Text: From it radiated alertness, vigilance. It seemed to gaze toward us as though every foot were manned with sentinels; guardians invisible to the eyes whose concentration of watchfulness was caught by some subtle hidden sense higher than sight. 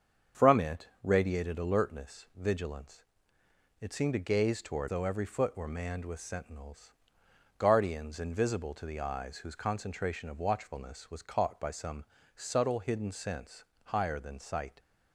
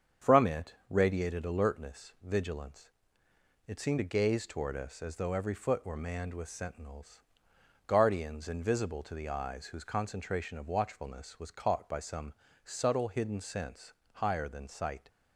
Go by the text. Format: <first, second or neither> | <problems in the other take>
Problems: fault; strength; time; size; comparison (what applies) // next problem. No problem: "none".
second | starts louder than the rest; strong; until 1.5 s; 7 dB; strong in the second // skips "us as"; at 4.8 s // pauses between "some" and "subtle"; slight; at 12.0 s; 0.32 s long; slight in the second // pauses between "sense" and "higher"; slight; at 13.6 s; 0.18 s long; slight in the second